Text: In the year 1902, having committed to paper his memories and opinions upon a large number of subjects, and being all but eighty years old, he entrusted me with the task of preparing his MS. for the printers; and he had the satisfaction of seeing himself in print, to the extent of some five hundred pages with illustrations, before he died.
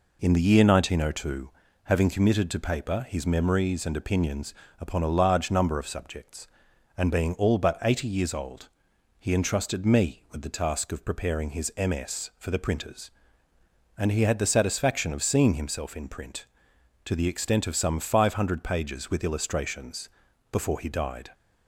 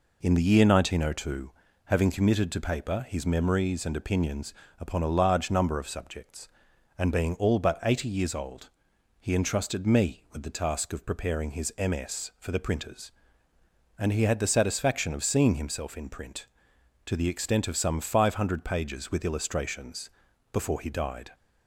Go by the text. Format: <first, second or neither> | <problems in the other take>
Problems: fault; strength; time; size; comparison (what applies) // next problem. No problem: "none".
neither | pauses between "opinions" and "upon"; slight; the same in both